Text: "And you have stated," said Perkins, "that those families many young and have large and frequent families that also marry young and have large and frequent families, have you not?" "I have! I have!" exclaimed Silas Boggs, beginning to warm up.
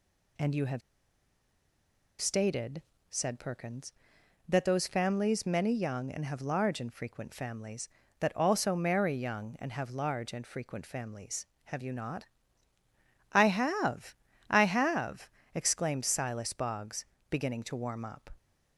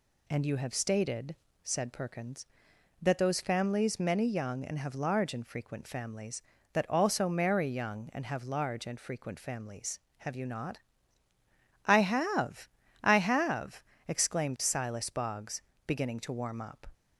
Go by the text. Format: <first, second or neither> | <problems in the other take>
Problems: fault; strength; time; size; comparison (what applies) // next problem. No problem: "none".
second | pauses between "have" and "stated"; strong; at 0.8 s; 1.4 s long